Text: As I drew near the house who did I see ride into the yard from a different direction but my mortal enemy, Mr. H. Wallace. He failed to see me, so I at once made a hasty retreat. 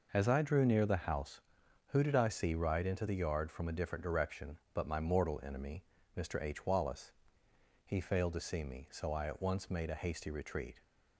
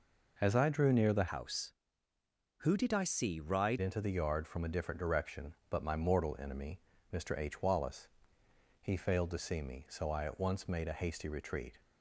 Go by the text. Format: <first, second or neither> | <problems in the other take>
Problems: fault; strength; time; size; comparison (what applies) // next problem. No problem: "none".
first | changes voice from "house" to "ride"; from 1.2 to 3.8 s; 2.6 s long